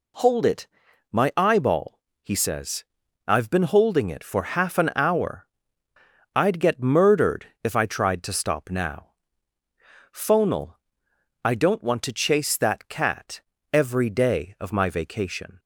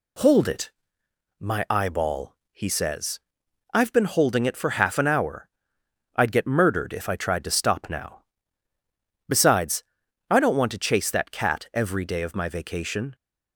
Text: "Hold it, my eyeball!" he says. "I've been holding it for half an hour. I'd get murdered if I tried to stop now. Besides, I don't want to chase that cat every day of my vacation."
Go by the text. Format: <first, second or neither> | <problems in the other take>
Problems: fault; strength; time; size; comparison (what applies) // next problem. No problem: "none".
second | pauses between "murdered" and "if"; slight; at 7.4 s; 0.18 s long // says "Phonal" for "Besides"; at 10.1 s // pauses between "cat" and "every"; slight; at 13.4 s; 0.32 s long